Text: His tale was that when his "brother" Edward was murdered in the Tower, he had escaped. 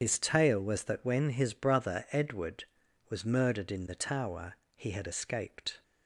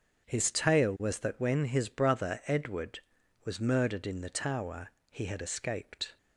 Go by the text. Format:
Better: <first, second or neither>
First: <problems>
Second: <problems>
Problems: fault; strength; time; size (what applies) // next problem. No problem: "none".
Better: second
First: loses the start of "His"; at 0.0 s; 75 ms // starts louder than the rest; strong; until 1.0 s; 8 dB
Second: starts louder than the rest; strong; until 1.3 s; 8 dB